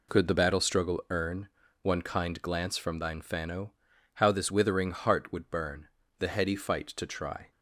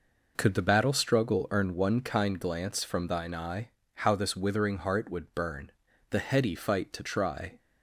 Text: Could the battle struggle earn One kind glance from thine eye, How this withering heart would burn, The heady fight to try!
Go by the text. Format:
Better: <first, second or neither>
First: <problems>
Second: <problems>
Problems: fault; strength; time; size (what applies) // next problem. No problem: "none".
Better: second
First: pauses between "earn" and "One"; slight; at 1.4 s; 0.34 s long // says "fano" for "eye"; at 3.2 s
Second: none